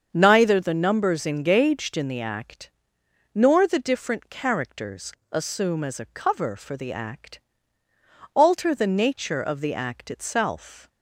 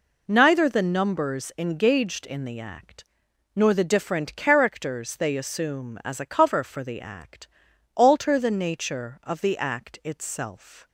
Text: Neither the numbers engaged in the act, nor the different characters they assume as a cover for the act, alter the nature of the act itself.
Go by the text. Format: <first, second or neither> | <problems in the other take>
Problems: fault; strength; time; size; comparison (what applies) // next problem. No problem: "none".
second | starts louder than the rest; until 1.1 s; 7 dB // skips "they"; at 5.2 s